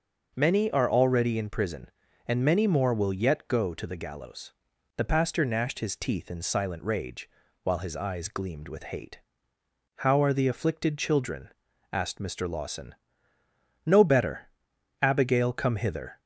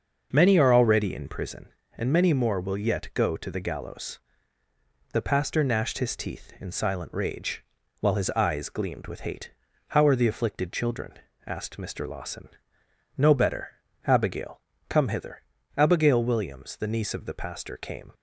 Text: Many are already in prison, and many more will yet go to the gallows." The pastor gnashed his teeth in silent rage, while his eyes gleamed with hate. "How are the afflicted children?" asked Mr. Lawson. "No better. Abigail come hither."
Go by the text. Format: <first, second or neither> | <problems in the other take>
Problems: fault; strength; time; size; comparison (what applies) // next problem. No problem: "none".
first | starts louder than the rest; until 1.3 s; 6 dB // pauses between "Abigail" and "come"; slight; at 14.6 s; 0.26 s long // goes on to say "Abigail Williams the niece of the pastor came"; strong; from 15.7 s on; 2.3 s long